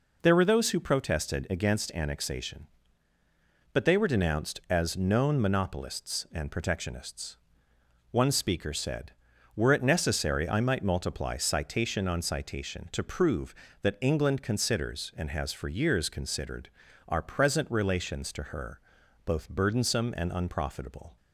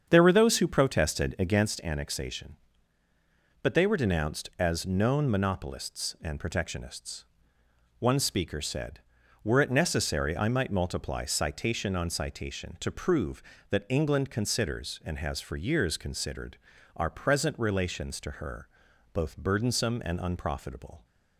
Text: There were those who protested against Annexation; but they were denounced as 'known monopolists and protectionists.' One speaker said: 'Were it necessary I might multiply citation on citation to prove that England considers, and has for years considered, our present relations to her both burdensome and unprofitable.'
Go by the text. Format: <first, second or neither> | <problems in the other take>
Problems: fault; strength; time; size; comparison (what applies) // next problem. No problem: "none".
first | starts louder than the rest; strong; until 1.8 s; 7.5 dB // pauses between "her" and "both"; noticeable; at 18.6 s; 0.46 s long; noticeable in the first